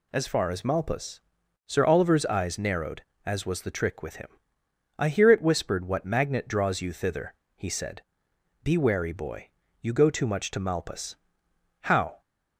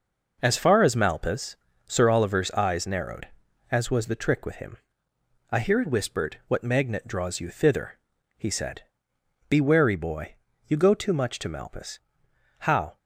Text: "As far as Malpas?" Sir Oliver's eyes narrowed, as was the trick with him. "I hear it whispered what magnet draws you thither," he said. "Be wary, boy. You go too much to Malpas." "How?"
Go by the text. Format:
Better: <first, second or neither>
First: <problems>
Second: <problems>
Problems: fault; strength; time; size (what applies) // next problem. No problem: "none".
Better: neither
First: none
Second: none